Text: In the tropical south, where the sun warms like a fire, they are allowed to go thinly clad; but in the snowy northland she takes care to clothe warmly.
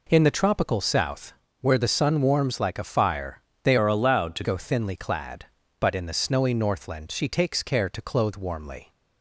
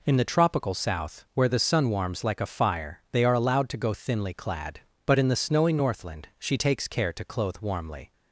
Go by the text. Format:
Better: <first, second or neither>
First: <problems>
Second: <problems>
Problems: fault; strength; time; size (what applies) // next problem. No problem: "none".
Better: second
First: changes voice from "are" to "to"; from 3.7 to 4.4 s; 0.7 s long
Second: none